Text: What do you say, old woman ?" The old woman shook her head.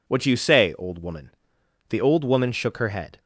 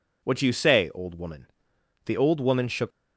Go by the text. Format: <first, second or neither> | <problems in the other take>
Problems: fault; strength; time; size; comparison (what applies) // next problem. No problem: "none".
first | stops before "her head"; at 2.9 s